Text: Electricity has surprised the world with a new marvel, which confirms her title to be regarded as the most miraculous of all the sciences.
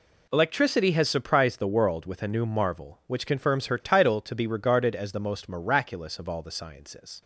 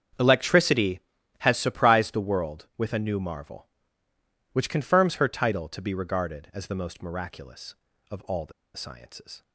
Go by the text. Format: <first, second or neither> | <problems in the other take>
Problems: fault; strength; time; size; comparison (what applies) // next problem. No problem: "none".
first | starts louder than the rest; strong; until 1.6 s; 7.5 dB // pauses between "the" and "sciences"; slight; at 8.5 s; 0.23 s long